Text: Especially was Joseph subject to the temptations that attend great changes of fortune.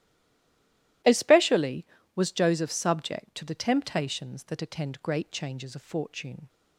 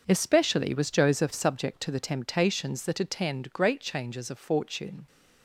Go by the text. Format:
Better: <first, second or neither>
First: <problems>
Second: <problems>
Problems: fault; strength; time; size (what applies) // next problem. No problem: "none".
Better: second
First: stays silent before the first word; until 1.0 s; 1.0 s long // starts louder than the rest; strong; until 2.3 s; 14.5 dB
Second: starts louder than the rest; until 1.0 s; 6.5 dB